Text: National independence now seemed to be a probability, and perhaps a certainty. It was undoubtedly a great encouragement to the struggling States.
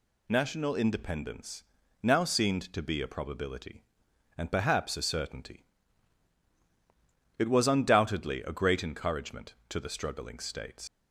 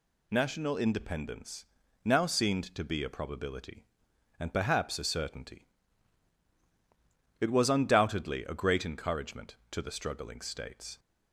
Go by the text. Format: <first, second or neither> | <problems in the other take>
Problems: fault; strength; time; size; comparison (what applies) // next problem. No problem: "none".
second | pauses between "independence" and "now"; at 1.6 s; 0.38 s long; also in the second // leaves "States" unfinished; at 10.8 s; 95 ms